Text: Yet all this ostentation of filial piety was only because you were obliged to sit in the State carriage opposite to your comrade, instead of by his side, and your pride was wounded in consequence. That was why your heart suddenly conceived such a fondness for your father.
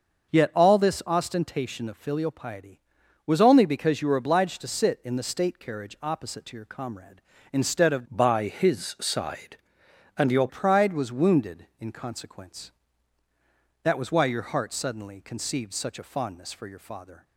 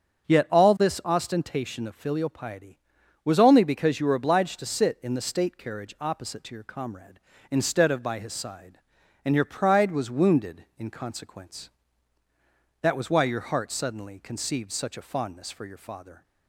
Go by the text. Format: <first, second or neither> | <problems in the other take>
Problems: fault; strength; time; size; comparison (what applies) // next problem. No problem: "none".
second | starts louder than the rest; until 1.3 s; 6 dB; also in the second // changes voice from "by" to "your"; from 8.1 to 10.4 s; 2.3 s long